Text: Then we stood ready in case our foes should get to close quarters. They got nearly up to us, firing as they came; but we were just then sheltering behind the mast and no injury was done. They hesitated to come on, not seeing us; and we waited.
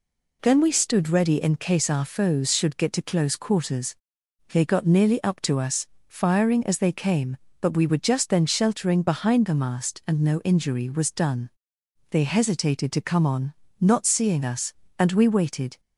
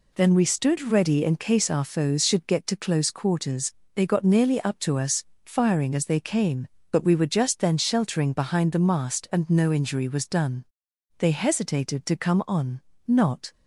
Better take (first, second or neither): first